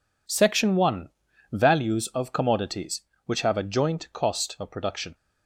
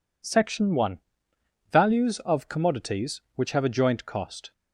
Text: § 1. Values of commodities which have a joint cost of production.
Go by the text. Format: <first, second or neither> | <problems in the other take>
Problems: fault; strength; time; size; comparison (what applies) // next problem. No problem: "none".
first | stops before "of production"; at 4.5 s